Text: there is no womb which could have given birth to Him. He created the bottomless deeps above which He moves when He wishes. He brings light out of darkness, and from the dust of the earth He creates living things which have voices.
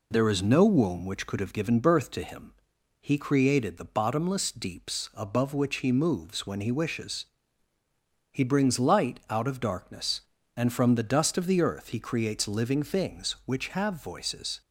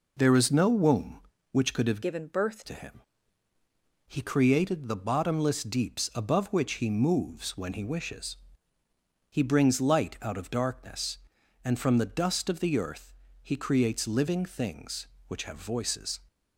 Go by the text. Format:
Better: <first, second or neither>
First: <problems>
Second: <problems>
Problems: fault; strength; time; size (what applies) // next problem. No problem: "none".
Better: first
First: none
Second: changes voice from "given" to "birth"; from 2.0 to 2.6 s; 0.6 s long // pauses between "earth" and "He"; slight; at 13.1 s; 0.28 s long